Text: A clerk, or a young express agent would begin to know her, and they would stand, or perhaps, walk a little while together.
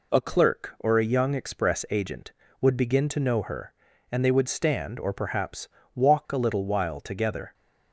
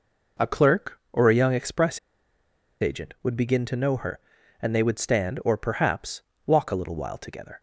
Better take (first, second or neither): first